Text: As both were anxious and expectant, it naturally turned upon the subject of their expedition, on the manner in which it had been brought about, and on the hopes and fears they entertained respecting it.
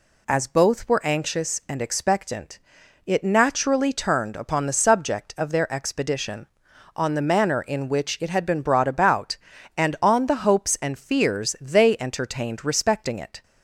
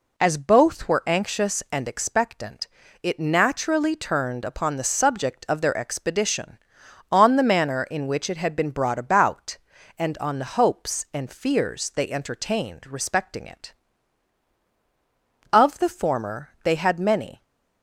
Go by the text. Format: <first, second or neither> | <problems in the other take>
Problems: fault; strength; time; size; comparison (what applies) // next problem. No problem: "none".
first | goes on to say "Of the former they had many"; strong; from 15.5 s on; 1.9 s long